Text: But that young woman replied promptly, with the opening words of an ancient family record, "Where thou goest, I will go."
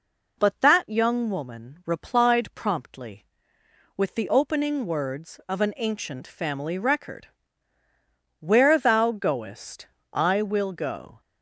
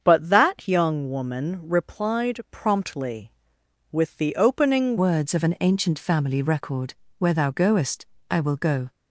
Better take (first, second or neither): first